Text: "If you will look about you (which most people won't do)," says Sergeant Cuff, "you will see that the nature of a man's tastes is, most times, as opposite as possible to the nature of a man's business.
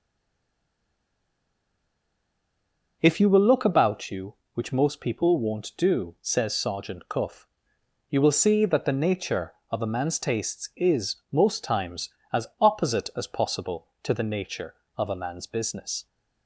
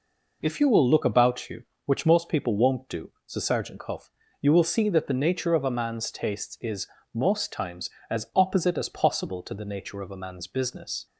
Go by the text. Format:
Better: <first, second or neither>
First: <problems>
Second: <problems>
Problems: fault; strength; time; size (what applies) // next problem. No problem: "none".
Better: second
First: stays silent before the first word; strong; until 3.0 s; 3.0 s long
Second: none